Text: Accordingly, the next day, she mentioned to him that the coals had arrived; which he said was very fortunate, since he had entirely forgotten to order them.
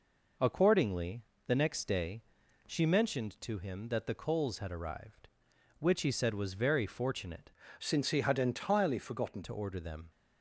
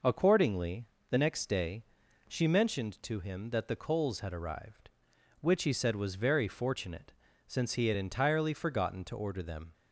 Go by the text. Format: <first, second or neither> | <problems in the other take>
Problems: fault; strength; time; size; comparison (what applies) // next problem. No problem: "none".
second | changes voice from "since" to "forgotten"; from 7.7 to 9.4 s; 1.7 s long